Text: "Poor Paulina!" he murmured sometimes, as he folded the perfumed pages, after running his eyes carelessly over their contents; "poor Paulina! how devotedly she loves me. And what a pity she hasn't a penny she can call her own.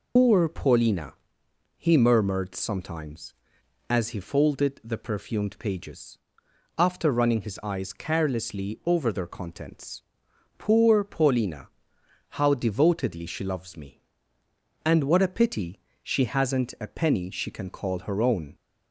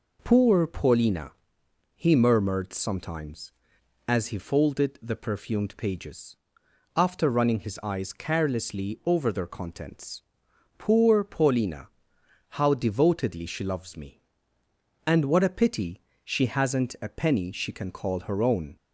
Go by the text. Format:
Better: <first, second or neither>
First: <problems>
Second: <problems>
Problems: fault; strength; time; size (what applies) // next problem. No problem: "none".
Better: second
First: loses the start of "Poor"; at 0.1 s; 145 ms // pauses between "pity" and "she"; slight; at 15.8 s; 0.20 s long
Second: pauses between "pity" and "she"; slight; at 16.0 s; 0.20 s long